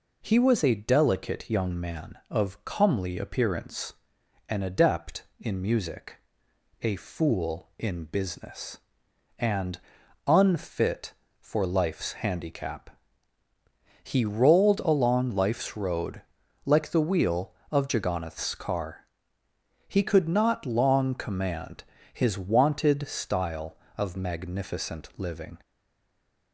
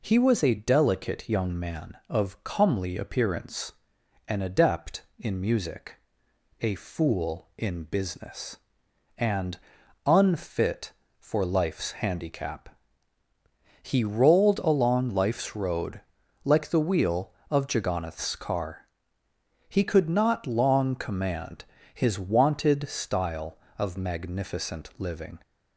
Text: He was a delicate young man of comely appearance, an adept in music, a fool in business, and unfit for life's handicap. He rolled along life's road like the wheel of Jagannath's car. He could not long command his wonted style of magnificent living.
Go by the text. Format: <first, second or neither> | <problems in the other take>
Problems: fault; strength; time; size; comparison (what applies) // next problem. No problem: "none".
second | pauses between "and" and "unfit"; noticeable; at 9.7 s; 0.48 s long; noticeable in the second // pauses between "road" and "like"; at 16.2 s; 0.44 s long; also in the second // pauses between "command" and "his"; slight; at 21.8 s; 0.28 s long; slight in the second // stays silent after the last word; slight; from 25.6 s on; 0.9 s long